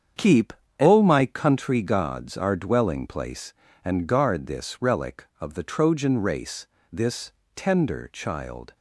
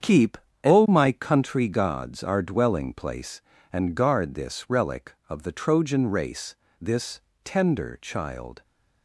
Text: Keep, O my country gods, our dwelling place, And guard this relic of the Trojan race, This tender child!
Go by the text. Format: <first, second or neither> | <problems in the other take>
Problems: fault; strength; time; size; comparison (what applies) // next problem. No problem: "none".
neither | starts louder than the rest; strong; the same in both // pauses between "This" and "tender"; slight; the same in both